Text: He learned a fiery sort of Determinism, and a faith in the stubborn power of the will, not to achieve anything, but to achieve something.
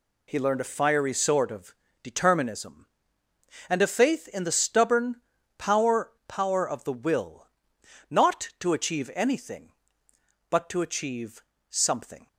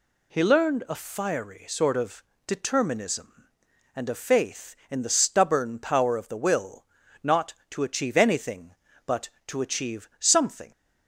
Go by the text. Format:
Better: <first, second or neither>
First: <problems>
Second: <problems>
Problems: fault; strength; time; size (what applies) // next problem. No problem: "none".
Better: second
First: pauses between "of" and "Determinism"; slight; at 1.7 s; 0.30 s long // pauses between "stubborn" and "power"; at 5.1 s; 0.42 s long // says "power" twice; at 6.2 s // pauses between "achieve" and "something"; slight; at 11.4 s; 0.30 s long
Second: pauses between "of" and "Determinism"; slight; at 2.2 s; 0.24 s long